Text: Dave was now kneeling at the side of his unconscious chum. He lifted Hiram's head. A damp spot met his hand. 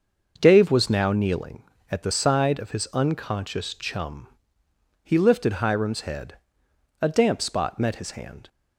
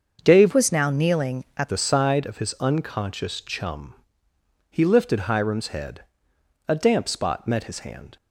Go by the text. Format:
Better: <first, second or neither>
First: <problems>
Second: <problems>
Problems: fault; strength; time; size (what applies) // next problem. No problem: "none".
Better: first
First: starts louder than the rest; noticeable; until 1.4 s; 6 dB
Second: starts louder than the rest; until 1.2 s; 6.5 dB // changes voice from "was" to "at"; from 0.5 to 1.6 s; 1.1 s long